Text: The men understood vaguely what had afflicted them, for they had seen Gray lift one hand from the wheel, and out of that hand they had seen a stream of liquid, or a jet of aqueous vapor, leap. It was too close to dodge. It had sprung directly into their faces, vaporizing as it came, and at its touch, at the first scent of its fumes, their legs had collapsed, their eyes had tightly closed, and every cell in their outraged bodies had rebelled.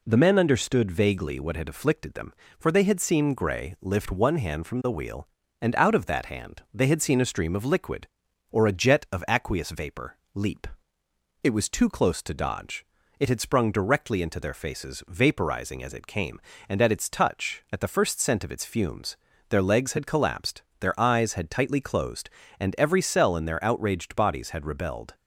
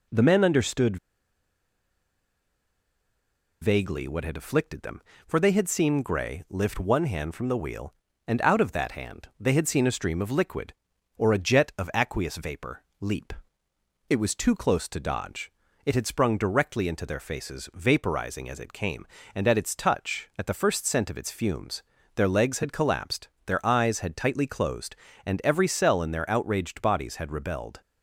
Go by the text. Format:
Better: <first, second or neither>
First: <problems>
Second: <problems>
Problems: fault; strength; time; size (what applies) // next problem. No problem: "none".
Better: first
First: none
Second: pauses between "understood" and "vaguely"; strong; at 0.9 s; 2.6 s long